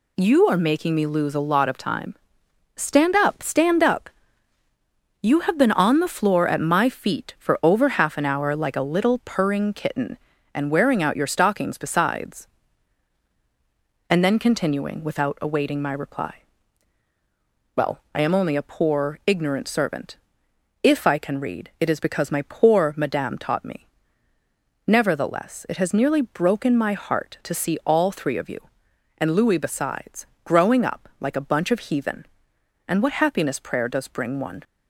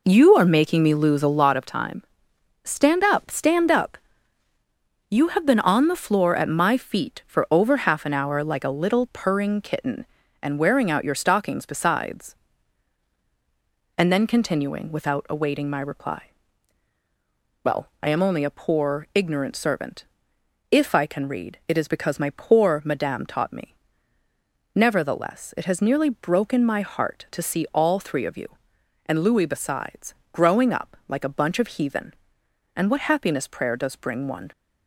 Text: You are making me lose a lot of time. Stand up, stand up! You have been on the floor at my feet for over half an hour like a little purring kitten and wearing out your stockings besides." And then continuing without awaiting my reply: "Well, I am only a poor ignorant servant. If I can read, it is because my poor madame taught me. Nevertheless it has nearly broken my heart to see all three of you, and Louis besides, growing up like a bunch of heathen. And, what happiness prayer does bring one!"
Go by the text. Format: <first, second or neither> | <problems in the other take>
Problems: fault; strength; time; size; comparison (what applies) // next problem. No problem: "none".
first | starts louder than the rest; noticeable; until 1.6 s; 4 dB